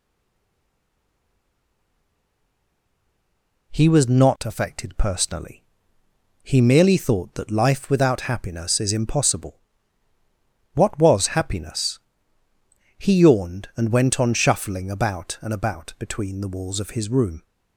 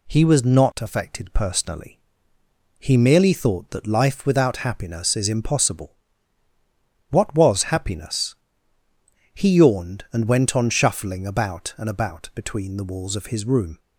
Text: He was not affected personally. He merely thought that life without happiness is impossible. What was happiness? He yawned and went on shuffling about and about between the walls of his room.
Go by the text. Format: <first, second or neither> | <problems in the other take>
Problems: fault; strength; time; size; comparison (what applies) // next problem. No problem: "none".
second | stays silent before the first word; strong; until 3.7 s; 3.7 s long